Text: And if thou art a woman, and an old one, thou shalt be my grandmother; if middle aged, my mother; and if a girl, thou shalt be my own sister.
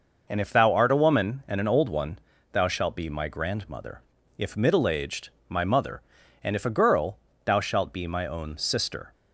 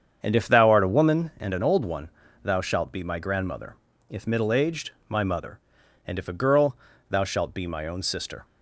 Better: first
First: none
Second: starts louder than the rest; strong; until 1.2 s; 7.5 dB

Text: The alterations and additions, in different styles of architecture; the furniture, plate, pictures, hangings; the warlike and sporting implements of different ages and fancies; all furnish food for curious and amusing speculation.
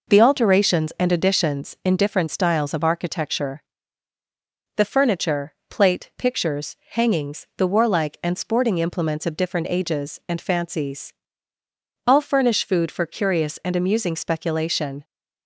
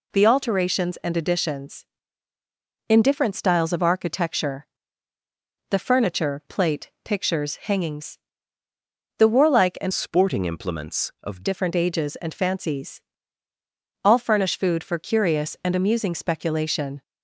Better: first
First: none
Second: changes voice from "sporting" to "of"; from 9.9 to 11.4 s; 1.5 s long

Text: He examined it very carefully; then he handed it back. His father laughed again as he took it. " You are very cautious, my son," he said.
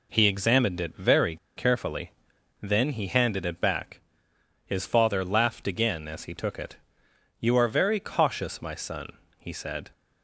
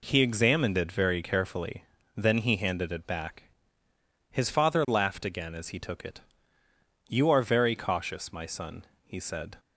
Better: second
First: pauses between "very" and "carefully"; slight; at 1.3 s; 0.20 s long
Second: none

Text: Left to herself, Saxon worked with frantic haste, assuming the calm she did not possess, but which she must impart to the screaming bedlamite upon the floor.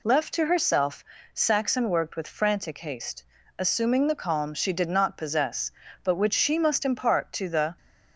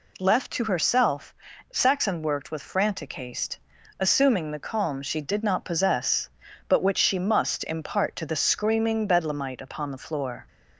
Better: second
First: stops before "screaming bedlamite upon the floor"; at 7.7 s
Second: none

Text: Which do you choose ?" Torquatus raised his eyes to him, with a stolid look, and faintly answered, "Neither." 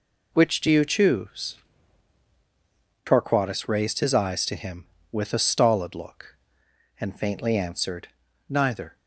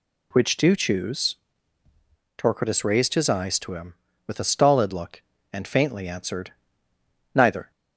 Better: first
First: none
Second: skips "you"; at 0.7 s

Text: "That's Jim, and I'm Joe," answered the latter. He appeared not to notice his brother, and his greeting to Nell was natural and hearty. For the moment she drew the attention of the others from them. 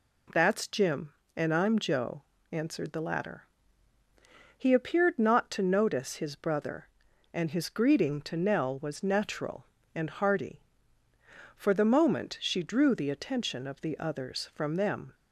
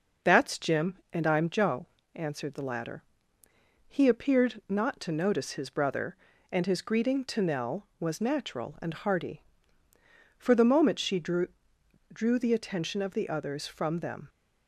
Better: first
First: none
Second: says "drew" twice; at 12.1 s

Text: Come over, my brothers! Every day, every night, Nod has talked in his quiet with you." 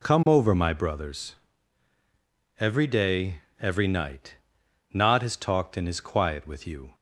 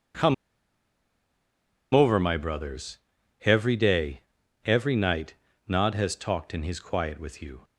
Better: first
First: none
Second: pauses between "Come" and "over"; strong; at 0.3 s; 1.6 s long

